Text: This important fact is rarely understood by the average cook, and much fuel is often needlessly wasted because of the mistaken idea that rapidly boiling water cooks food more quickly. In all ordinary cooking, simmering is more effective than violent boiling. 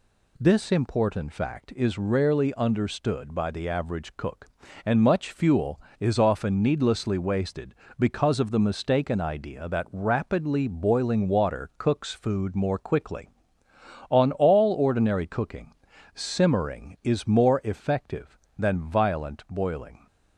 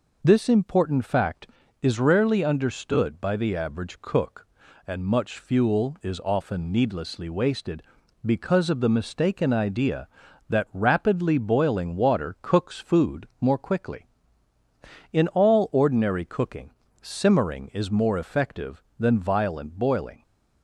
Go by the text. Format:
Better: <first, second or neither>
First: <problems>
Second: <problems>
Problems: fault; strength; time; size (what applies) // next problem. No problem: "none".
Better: second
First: says "On" for "In"; at 14.1 s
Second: none